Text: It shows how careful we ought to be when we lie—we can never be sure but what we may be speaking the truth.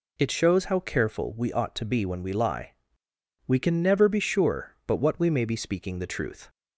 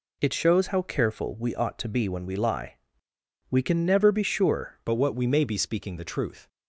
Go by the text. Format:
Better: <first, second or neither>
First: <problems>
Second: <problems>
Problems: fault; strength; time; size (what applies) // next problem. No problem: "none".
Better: first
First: none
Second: changes voice at "but"; from 4.8 s on; 1.6 s long